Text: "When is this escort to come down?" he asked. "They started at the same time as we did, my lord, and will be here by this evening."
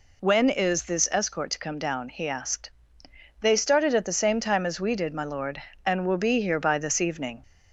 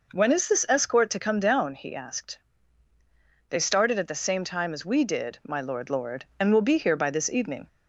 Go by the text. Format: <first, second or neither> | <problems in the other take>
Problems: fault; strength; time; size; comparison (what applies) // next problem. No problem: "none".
first | says "lord" twice; at 5.8 s